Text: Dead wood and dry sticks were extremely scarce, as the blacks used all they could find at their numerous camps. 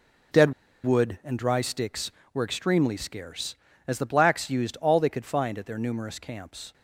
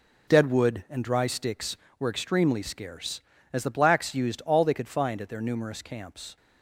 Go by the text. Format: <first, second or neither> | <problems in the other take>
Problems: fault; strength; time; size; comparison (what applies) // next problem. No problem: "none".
second | pauses between "Dead" and "wood"; slight; at 0.5 s; 0.31 s long